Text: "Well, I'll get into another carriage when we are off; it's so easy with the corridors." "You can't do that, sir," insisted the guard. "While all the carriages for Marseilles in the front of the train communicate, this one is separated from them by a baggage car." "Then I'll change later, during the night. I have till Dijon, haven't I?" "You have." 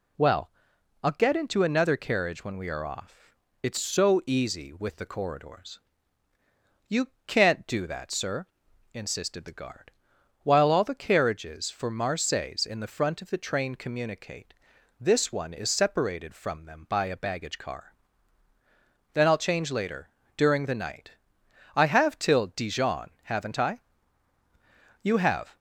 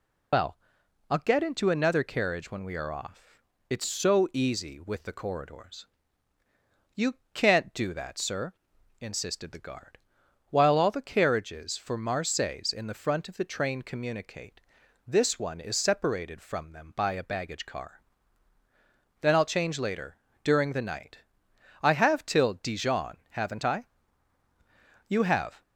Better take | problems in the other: first | loses the start of "Well"; at 0.3 s; 90 ms // pauses between "You" and "can't"; slight; at 7.1 s; 0.18 s long; slight in the first

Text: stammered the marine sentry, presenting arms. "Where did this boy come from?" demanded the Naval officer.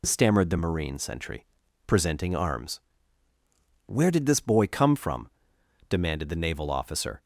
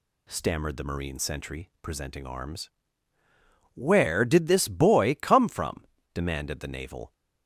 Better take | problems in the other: first | stops before "officer"; at 7.1 s

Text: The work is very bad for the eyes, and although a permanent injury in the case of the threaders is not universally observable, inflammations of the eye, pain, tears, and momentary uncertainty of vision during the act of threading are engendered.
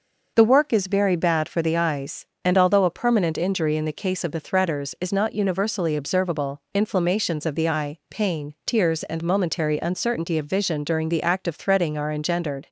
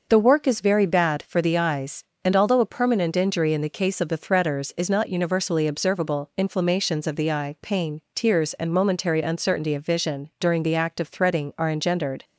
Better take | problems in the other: neither | none

